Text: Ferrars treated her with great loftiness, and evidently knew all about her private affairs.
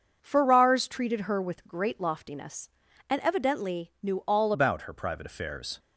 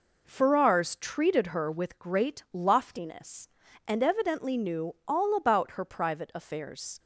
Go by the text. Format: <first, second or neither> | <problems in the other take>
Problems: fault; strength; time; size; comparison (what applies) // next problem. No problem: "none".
second | starts louder than the rest; until 1.2 s; 6.5 dB // changes voice at "about"; from 4.5 s on; 1.2 s long